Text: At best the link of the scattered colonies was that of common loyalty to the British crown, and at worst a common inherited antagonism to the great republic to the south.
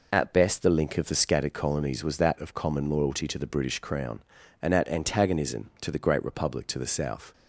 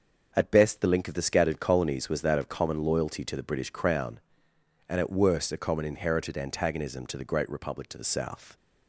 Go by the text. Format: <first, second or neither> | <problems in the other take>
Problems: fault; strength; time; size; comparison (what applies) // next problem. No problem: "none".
second | skips "worst a common inherited"; at 4.8 s